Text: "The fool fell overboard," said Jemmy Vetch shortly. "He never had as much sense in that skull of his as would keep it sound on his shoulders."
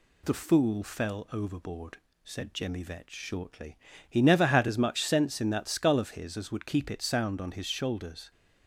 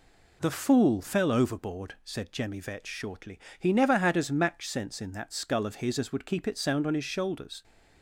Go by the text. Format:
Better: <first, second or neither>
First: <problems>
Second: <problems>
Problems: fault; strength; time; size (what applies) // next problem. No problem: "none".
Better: first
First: none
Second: says "match" for "much"; at 4.3 s